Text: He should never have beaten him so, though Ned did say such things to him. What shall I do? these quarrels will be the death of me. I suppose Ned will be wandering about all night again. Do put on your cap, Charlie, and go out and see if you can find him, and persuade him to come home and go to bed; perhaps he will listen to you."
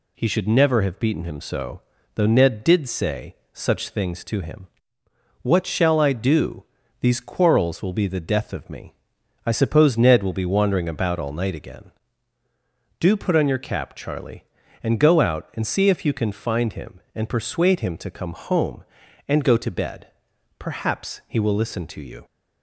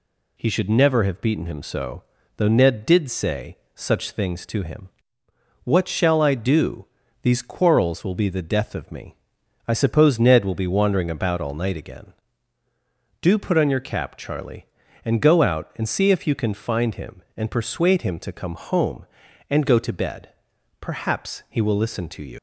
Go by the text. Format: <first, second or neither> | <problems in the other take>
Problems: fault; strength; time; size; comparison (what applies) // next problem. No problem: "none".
first | pauses between "say" and "such"; slight; at 3.5 s; 0.16 s long; slight in the first // leaves "you" unfinished; at 22.3 s; 80 ms